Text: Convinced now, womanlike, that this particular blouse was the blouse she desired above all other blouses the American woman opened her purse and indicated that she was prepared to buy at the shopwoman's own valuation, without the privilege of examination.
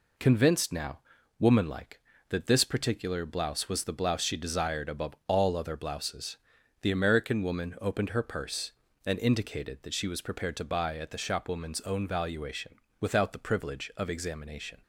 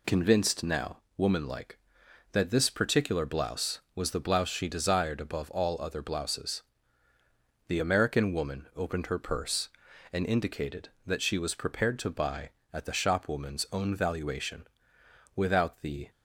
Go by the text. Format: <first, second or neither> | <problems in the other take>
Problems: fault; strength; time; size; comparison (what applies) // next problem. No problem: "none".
first | pauses between "blouses" and "the"; at 6.6 s; 1.0 s long; also in the first // stops before "privilege of examination"; at 16.0 s